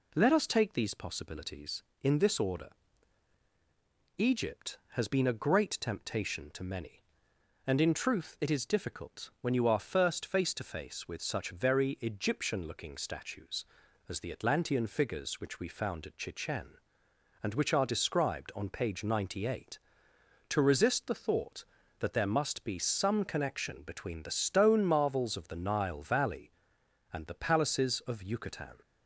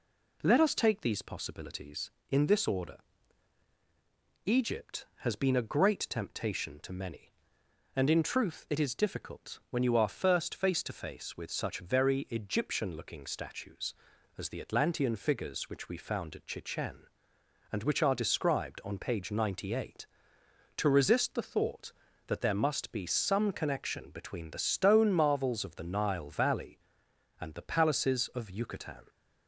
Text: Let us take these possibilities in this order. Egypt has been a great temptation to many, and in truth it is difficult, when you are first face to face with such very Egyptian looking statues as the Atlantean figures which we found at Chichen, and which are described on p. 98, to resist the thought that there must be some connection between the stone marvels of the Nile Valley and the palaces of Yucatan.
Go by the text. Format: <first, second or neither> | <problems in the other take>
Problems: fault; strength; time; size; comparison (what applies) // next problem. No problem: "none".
neither | none